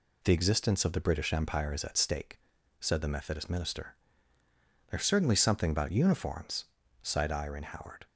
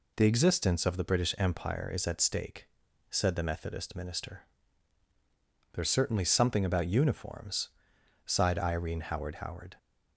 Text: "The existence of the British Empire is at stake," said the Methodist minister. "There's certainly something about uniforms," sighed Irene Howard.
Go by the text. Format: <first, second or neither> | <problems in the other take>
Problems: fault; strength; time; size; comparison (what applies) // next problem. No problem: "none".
first | says "Howard" twice; at 9.3 s